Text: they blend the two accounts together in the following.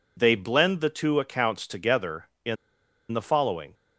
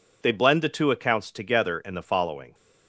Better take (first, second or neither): second